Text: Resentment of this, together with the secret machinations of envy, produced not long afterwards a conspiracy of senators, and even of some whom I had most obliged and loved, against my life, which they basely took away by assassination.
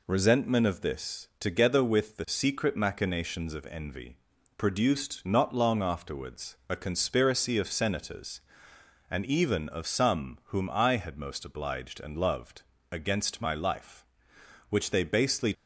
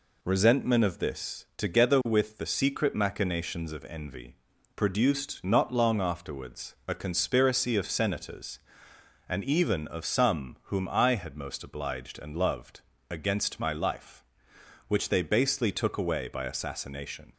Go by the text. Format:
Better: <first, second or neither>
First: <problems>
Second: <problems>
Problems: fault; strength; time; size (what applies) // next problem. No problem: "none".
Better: second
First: stops before "took away by assassination"; at 15.5 s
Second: none